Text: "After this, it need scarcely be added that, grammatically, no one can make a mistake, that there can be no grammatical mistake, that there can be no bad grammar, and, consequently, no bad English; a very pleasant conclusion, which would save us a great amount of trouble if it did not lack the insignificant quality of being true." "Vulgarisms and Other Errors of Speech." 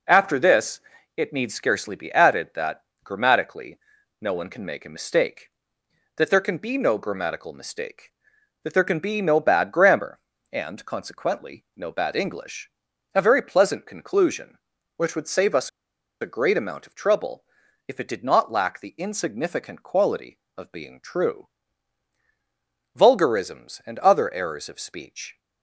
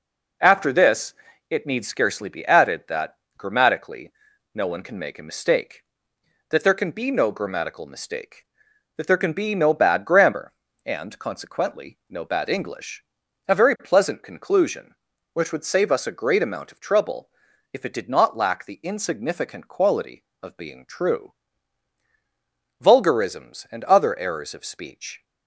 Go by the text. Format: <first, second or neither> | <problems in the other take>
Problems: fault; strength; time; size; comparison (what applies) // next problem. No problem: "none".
second | pauses between "us" and "a"; noticeable; at 15.6 s; 0.52 s long // pauses between "trouble" and "if"; at 17.4 s; 0.42 s long; also in the second